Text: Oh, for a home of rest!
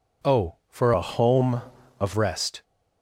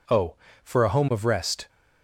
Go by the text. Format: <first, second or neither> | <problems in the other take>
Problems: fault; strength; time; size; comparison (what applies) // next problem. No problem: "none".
second | changes voice from "a" to "of"; from 0.9 to 2.1 s; 1.2 s long